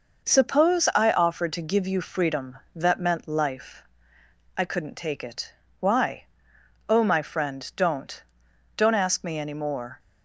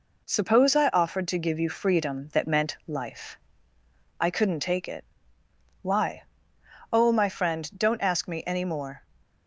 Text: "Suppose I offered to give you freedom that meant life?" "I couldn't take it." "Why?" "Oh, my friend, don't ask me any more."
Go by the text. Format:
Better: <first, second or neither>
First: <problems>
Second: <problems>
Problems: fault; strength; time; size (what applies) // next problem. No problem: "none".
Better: second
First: says "don't" twice; at 8.7 s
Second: none